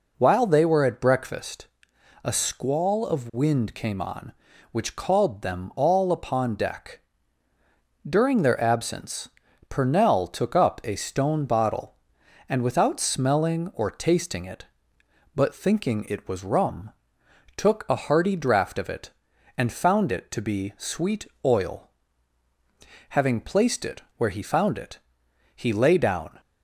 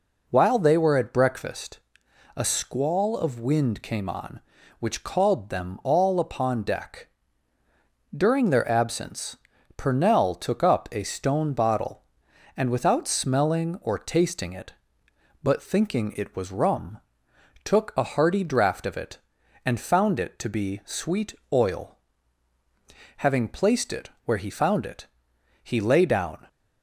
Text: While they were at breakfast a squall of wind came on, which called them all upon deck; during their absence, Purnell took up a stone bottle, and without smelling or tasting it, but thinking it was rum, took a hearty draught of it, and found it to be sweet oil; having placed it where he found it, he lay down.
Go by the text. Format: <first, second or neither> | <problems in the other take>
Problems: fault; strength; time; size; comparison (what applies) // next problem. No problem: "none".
neither | pauses between "breakfast" and "a"; noticeable; the same in both // pauses between "sweet" and "oil"; slight; the same in both